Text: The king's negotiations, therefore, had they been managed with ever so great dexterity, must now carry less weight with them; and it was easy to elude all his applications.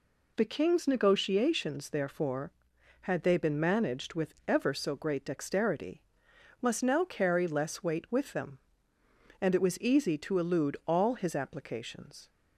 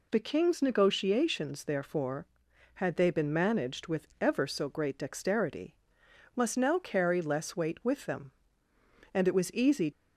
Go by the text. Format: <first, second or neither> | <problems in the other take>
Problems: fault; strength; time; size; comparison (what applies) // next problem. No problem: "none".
first | stops before "to elude all his applications"; at 9.9 s